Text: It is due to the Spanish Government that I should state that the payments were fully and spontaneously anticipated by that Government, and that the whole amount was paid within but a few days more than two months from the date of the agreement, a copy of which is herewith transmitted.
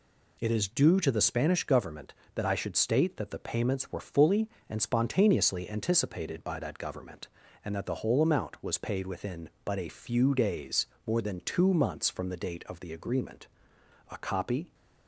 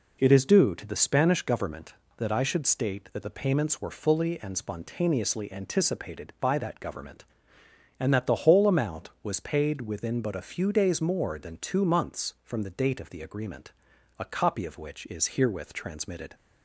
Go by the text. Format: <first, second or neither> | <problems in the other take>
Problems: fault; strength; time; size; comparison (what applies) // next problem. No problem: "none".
second | pauses between "days" and "more"; slight; at 10.8 s; 0.18 s long // stops before "of which is herewith transmitted"; at 14.7 s